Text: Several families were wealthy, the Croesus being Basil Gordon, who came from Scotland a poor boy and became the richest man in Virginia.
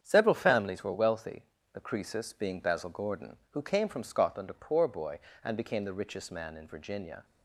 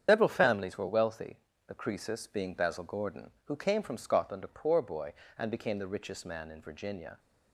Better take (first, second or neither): first